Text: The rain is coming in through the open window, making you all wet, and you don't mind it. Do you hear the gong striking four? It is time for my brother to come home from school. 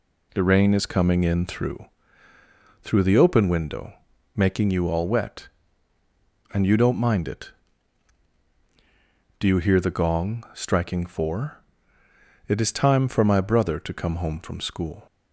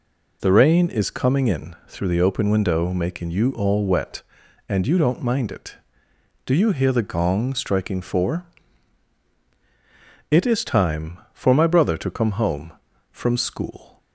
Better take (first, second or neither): second